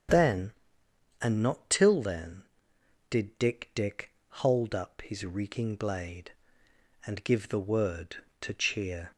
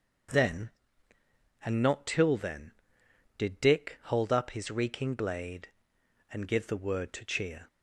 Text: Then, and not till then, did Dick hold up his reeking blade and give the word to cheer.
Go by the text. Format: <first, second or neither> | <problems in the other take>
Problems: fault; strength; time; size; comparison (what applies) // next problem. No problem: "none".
second | starts louder than the rest; until 1.7 s; 7 dB; also in the second // says "Dick" twice; at 3.7 s